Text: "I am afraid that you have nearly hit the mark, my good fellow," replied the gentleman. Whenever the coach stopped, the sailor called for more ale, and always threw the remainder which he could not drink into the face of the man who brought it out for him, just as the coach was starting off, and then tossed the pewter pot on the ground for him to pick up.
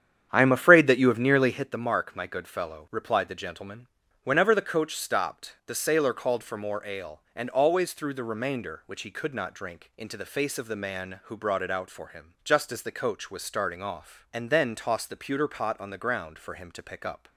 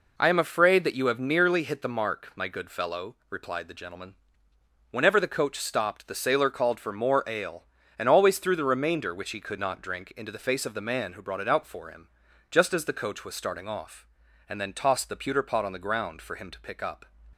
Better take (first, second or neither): second